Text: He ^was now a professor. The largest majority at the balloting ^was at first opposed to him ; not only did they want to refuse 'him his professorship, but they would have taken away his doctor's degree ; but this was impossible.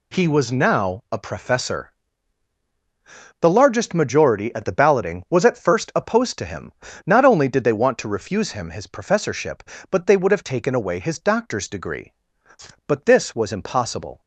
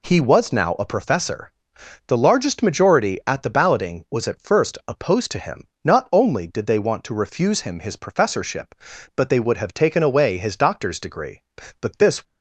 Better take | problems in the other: first | stops before "was impossible"; at 12.2 s

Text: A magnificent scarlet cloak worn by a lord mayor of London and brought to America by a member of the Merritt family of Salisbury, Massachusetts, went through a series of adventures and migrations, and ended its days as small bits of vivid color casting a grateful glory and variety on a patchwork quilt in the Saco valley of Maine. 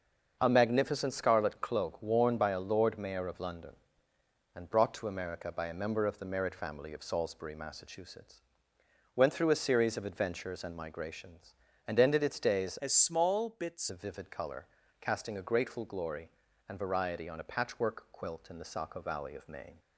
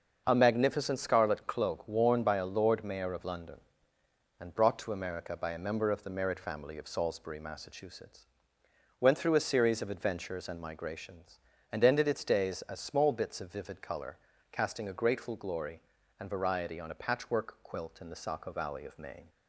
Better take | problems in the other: second | starts louder than the rest; until 1.4 s; 6.5 dB; also in the second // changes voice from "as" to "bits"; from 12.8 to 13.9 s; 1.1 s long // pauses between "color" and "casting"; slight; at 14.6 s; 0.34 s long; slight in the second

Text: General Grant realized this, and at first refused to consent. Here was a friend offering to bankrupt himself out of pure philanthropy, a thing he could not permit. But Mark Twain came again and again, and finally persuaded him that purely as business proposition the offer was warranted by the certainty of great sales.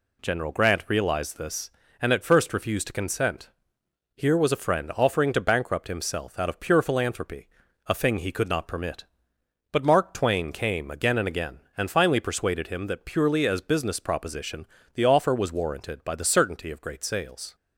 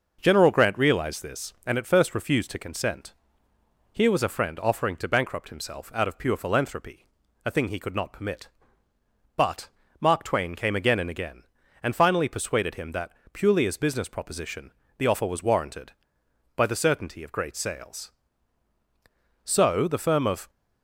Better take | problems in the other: first | pauses between "But" and "Mark"; slight; at 9.6 s; 0.30 s long // pauses between "that" and "purely"; slight; at 13.1 s; 0.20 s long // pauses between "proposition" and "the"; slight; at 14.7 s; 0.26 s long; slight in the first // goes on to say "So the firm of"; noticeable; from 19.5 s on; 0.94 s long

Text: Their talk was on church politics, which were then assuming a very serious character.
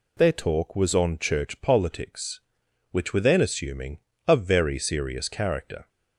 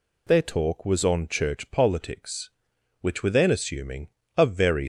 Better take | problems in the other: first | pauses between "assuming" and "a"; slight; at 4.0 s; 0.26 s long; slight in the first // stops before "serious character"; at 4.8 s

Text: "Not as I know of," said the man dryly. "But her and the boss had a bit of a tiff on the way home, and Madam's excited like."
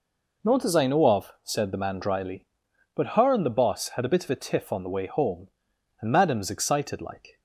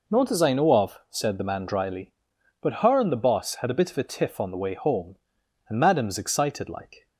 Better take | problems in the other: neither | none

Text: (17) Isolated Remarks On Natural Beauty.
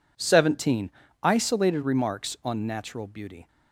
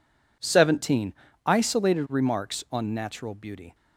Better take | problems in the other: neither | none

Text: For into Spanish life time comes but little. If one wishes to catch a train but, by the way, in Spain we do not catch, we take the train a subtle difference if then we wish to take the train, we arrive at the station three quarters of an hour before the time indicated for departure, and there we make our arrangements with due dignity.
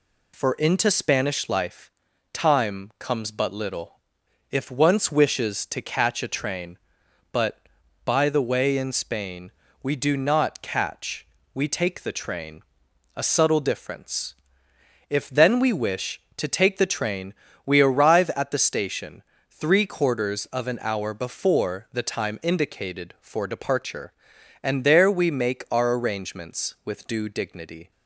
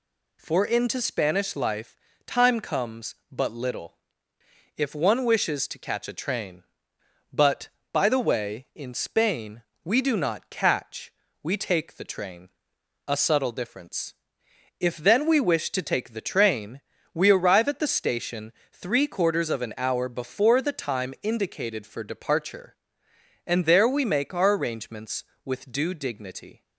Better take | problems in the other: second | pauses between "life" and "time"; at 1.9 s; 0.40 s long; slight in the second // says "once" for "one"; at 4.6 s // pauses between "Spain" and "we"; slight; at 9.5 s; 0.28 s long; slight in the second // pauses between "train" and "a"; noticeable; at 12.6 s; 0.52 s long; noticeable in the second // pauses between "difference" and "if"; noticeable; at 14.3 s; 0.74 s long; noticeable in the second // pauses between "station" and "three"; slight; at 19.2 s; 0.26 s long; slight in the second

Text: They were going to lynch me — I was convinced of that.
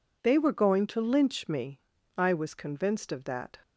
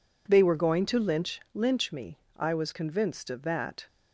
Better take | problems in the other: first | says "lynch" twice; at 1.5 s

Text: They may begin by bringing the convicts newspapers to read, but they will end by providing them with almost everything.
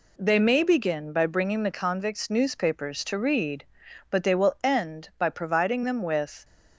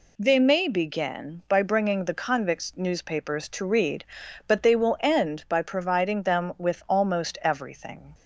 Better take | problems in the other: second | stops before "almost everything"; at 6.4 s

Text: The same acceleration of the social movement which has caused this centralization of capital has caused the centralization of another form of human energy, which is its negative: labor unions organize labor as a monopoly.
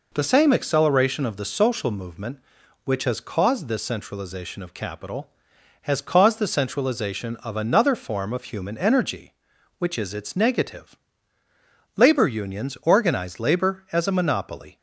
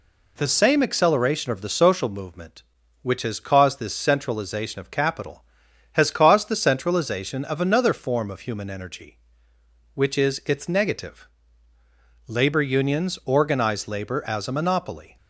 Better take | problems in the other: neither | none

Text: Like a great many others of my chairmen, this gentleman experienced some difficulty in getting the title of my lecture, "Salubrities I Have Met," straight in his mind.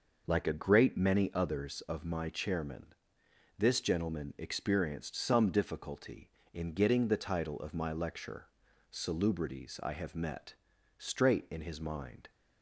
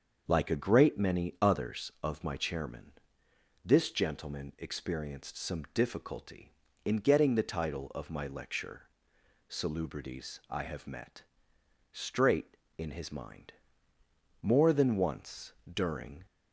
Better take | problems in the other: first | starts louder than the rest; until 1.2 s; 6.5 dB // goes on to say "More than once during"; strong; from 14.4 s on; 1.8 s long

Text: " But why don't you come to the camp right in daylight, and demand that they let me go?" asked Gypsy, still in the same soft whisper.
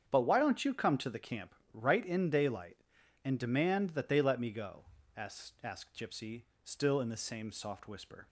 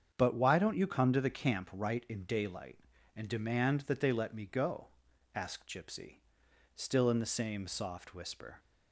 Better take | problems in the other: second | starts louder than the rest; strong; until 1.0 s; 8 dB; strong in the second // pauses between "camp" and "right"; slight; at 1.5 s; 0.20 s long // says "asked" twice; at 5.6 s

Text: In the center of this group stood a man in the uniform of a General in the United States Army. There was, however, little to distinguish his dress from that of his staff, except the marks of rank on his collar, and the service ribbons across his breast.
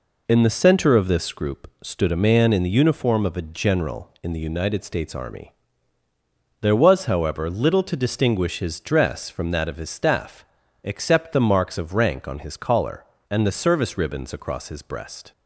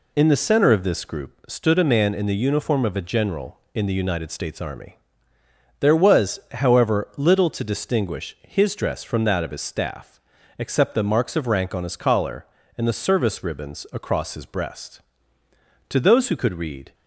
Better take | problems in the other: first | goes on to say "To those who could read"; noticeable; from 15.8 s on; 1.0 s long

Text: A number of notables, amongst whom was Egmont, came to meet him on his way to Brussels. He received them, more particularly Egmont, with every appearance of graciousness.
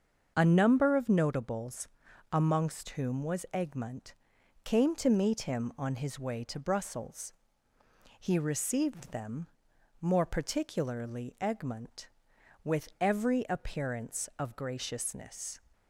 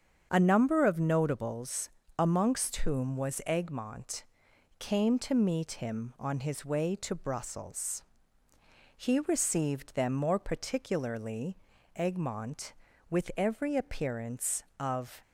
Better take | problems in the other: first | starts louder than the rest; strong; until 1.3 s; 7.5 dB; also in the first // pauses between "particularly" and "Egmont"; at 11.5 s; 0.38 s long // stops before "graciousness"; at 15.2 s

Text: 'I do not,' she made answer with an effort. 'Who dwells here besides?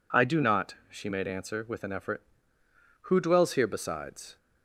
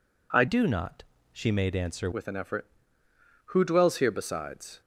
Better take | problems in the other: first | changes voice from "do" to "answer"; from 0.4 to 2.1 s; 1.7 s long

